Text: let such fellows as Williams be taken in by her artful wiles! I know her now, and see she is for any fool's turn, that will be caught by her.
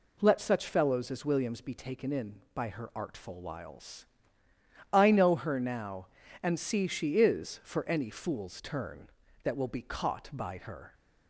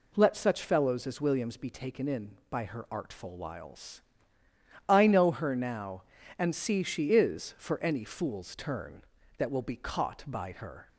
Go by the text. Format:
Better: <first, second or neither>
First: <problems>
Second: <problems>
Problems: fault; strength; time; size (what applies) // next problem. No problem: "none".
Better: neither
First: none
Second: none